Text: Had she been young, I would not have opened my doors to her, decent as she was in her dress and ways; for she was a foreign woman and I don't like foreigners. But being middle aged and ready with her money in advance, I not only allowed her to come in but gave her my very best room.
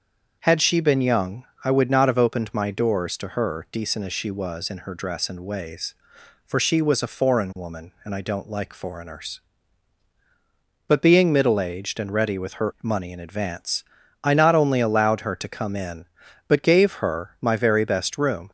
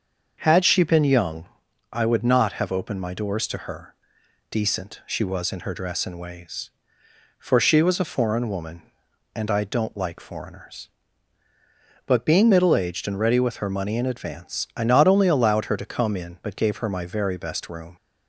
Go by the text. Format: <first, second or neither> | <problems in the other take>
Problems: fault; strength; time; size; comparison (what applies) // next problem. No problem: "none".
first | starts louder than the rest; until 1.4 s; 6.5 dB; also in the first // skips "as"; at 5.0 s